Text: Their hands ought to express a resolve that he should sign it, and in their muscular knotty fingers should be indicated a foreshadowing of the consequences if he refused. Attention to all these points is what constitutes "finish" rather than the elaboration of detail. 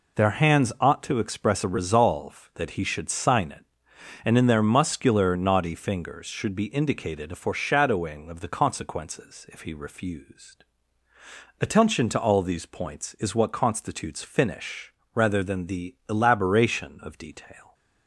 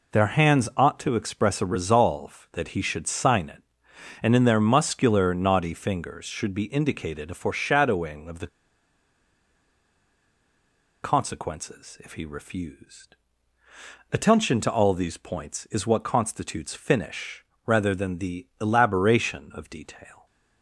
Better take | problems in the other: first | pauses between "the" and "consequences"; strong; at 8.4 s; 2.5 s long // pauses between "finish" and "rather"; slight; at 17.4 s; 0.20 s long; slight in the first

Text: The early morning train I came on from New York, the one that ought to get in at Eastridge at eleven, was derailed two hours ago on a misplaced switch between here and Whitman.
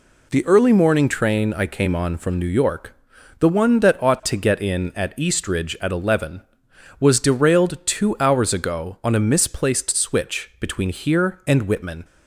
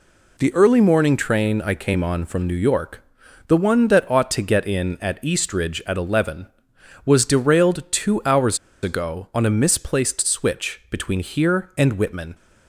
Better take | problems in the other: first | pauses between "hours" and "ago"; slight; at 8.5 s; 0.26 s long

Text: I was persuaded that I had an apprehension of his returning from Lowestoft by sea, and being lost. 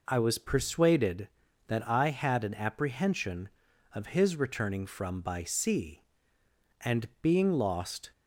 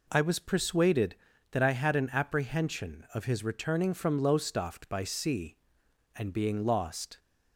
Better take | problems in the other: second | skips "Lowestoft"; at 5.1 s

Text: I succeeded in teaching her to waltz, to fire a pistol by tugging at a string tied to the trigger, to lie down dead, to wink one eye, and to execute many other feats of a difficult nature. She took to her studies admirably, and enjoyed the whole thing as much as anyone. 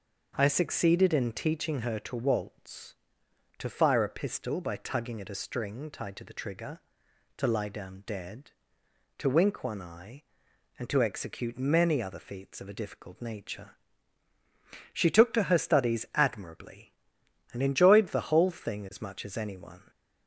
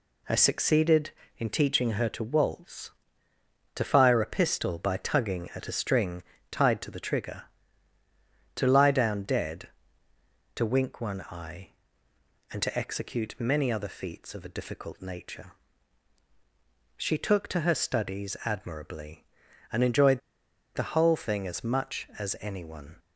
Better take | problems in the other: first | pauses between "string" and "tied"; slight; at 6.2 s; 0.28 s long // pauses between "enjoyed" and "the"; noticeable; at 20.2 s; 0.56 s long

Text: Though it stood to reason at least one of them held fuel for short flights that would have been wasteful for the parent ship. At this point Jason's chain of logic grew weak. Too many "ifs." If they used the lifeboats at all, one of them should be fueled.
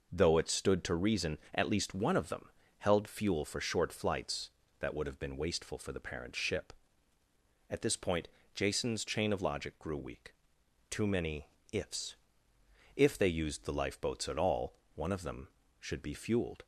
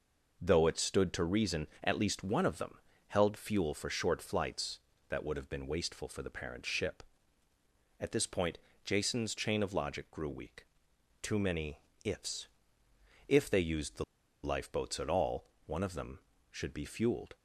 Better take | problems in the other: first | pauses between "them" and "held"; slight; at 2.7 s; 0.30 s long; slight in the first // pauses between "point" and "Jason's"; slight; at 8.5 s; 0.26 s long; slight in the first // pauses between "many" and "ifs"; slight; at 11.7 s; 0.24 s long; slight in the first // pauses between "the" and "lifeboats"; at 14.0 s; 0.40 s long

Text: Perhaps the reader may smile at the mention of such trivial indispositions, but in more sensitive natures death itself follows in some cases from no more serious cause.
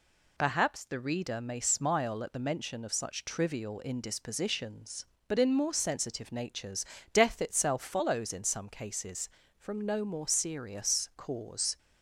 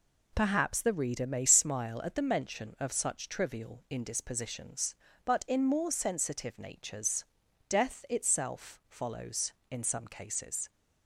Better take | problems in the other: first | pauses between "natures" and "death"; at 7.2 s; 0.42 s long; slight in the first // stops before "from no more serious cause"; at 10.7 s

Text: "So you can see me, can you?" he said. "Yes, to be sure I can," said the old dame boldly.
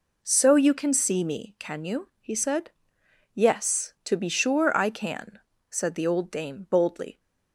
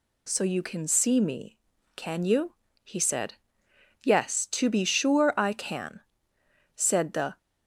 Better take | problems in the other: first | stops before "old dame boldly"; at 7.3 s

